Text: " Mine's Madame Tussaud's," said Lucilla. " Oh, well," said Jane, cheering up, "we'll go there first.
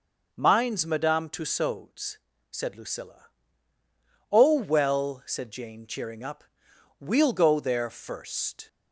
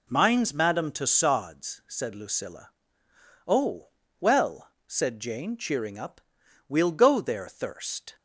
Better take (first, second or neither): first